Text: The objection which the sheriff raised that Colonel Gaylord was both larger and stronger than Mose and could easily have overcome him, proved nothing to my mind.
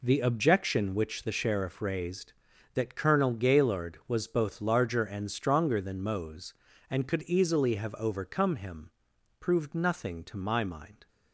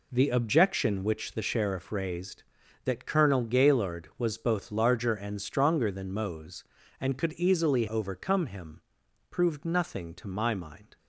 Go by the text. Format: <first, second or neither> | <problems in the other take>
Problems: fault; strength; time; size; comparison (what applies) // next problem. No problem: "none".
first | skips "have"; at 7.8 s